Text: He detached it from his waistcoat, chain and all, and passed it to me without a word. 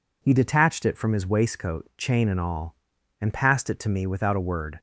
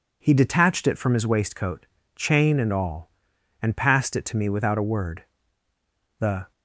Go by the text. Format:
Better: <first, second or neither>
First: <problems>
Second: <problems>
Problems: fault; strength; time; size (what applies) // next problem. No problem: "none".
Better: first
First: none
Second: goes on to say "The"; slight; from 6.1 s on; 0.32 s long